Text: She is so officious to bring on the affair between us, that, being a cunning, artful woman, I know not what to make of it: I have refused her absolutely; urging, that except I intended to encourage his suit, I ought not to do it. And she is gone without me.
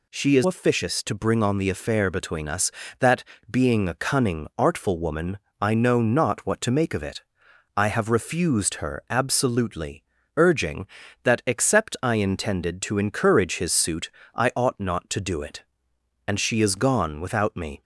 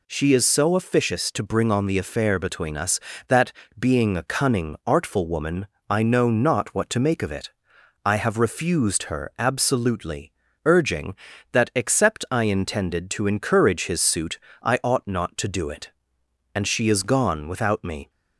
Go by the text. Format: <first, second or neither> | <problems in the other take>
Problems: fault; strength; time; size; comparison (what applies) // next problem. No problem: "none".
second | skips "so"; at 0.4 s